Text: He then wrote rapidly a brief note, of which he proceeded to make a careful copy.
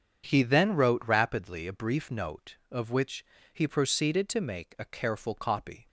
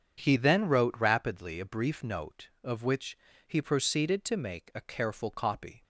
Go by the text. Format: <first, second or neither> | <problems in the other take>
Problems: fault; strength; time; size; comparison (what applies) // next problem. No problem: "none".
neither | starts louder than the rest; strong; the same in both // pauses between "which" and "he"; slight; the same in both